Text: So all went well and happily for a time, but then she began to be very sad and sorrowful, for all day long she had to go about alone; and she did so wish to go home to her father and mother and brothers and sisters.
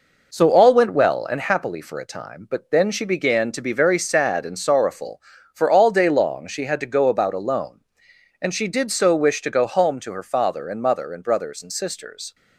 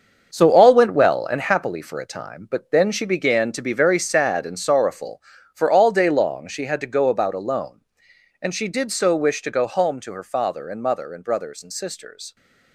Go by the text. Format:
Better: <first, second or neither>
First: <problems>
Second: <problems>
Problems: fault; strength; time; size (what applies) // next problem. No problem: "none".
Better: first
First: none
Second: gets quieter; strong; throughout; 9.5 dB